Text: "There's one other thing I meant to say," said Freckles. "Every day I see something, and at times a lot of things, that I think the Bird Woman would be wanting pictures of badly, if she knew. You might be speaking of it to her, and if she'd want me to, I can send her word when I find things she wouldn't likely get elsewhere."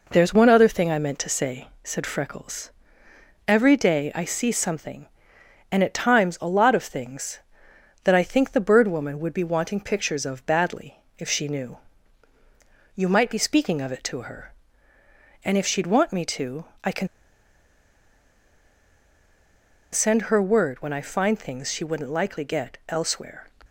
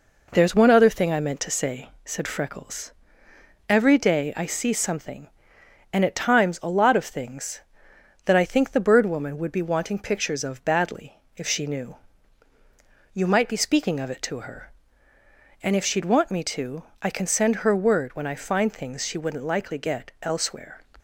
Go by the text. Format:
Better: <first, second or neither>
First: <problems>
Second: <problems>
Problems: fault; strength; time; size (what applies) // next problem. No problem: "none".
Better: second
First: pauses between "can" and "send"; strong; at 17.0 s; 2.8 s long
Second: none